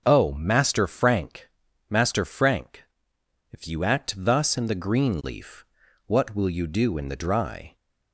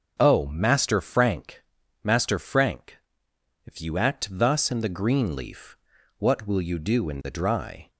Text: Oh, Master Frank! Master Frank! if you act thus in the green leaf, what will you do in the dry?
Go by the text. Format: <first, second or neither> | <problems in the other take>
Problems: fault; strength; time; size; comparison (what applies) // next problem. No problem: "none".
neither | starts louder than the rest; noticeable; the same in both